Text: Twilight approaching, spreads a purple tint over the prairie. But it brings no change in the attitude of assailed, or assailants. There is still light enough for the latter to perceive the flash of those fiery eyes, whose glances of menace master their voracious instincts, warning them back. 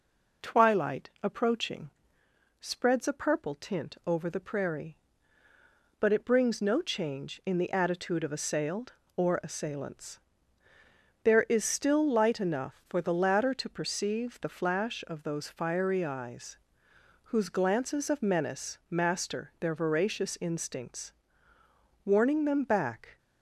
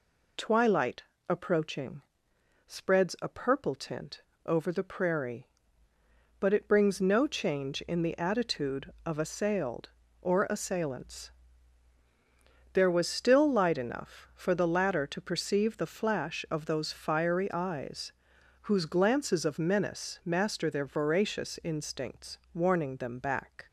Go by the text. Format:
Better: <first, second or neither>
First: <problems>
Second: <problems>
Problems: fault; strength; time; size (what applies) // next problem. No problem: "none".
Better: first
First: none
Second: pauses between "Twilight" and "approaching"; slight; at 1.0 s; 0.24 s long // pauses between "tint" and "over"; slight; at 4.2 s; 0.24 s long // says "was" for "is"; at 12.8 s